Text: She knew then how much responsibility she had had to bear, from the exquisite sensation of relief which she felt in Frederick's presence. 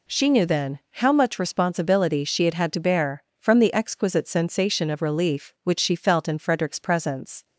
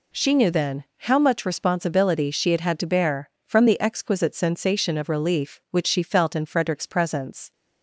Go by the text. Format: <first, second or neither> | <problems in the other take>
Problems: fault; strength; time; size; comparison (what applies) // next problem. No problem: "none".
neither | none